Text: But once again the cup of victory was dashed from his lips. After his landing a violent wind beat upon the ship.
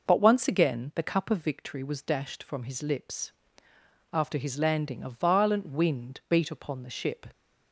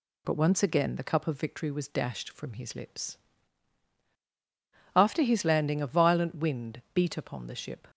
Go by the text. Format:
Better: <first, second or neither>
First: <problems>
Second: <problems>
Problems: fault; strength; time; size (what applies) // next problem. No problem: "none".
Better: neither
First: none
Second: none